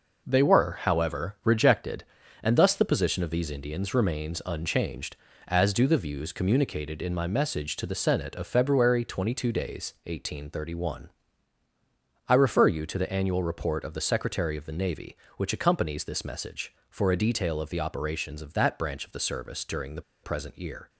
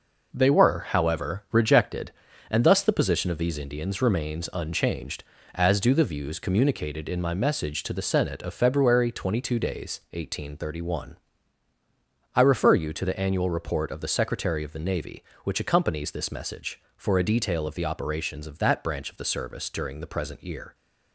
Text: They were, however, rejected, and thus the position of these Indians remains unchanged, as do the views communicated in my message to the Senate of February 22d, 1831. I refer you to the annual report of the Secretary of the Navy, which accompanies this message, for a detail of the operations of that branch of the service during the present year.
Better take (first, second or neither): second